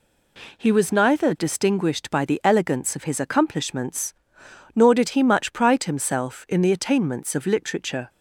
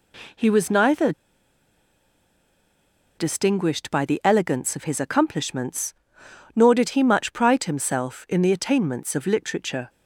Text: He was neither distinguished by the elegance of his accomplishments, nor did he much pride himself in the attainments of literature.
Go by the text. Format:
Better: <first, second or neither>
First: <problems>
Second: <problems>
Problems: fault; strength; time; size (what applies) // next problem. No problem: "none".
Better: first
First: none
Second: pauses between "neither" and "distinguished"; strong; at 1.1 s; 2.0 s long